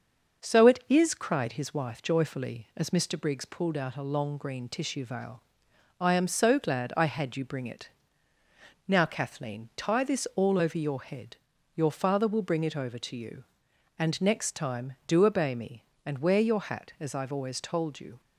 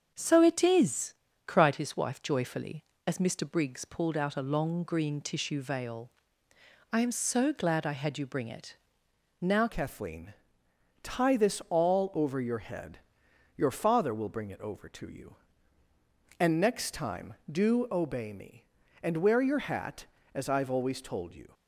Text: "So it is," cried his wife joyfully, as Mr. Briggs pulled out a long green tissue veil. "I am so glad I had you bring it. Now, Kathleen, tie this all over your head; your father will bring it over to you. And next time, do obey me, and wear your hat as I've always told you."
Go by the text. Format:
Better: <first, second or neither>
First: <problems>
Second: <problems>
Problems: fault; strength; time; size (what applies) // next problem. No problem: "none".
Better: first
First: none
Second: starts louder than the rest; until 1.1 s; 7 dB // changes voice at "Kathleen"; from 9.6 s on; 11.9 s long